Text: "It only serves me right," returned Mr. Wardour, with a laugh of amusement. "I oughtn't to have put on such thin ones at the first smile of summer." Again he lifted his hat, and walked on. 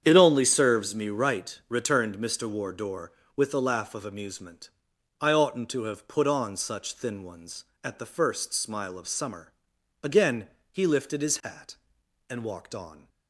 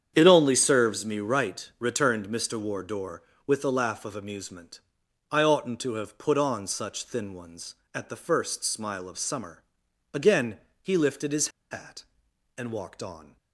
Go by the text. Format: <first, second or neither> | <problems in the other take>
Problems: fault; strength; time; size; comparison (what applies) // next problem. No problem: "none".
first | starts louder than the rest; strong; until 1.1 s; 8.5 dB; strong in the first // pauses between "Again" and "he"; slight; at 10.6 s; 0.20 s long; slight in the first // pauses between "his" and "hat"; slight; at 11.4 s; 0.22 s long